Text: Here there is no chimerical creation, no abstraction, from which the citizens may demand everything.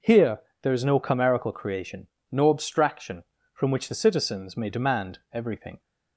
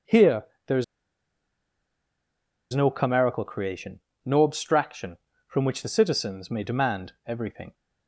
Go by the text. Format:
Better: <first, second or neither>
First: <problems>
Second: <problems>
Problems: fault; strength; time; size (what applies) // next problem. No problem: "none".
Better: first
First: pauses between "Here" and "there"; slight; at 0.4 s; 0.22 s long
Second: pauses between "Here" and "there"; slight; at 0.4 s; 0.22 s long // pauses between "is" and "no"; strong; at 0.8 s; 1.8 s long